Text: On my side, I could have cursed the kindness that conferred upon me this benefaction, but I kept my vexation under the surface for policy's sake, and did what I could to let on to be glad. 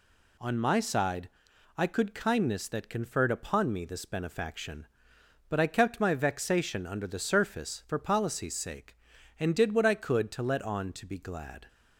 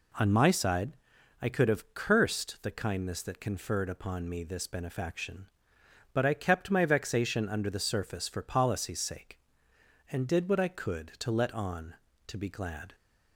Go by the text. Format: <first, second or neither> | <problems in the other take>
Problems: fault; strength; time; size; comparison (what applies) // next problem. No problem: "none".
second | skips "have cursed the"; at 2.1 s